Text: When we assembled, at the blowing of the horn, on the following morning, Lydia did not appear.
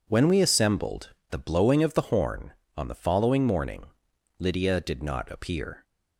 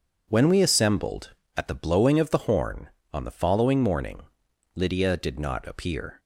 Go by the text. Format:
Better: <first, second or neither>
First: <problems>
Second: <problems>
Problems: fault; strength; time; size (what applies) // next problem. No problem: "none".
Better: second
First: skips "at"; at 1.2 s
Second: none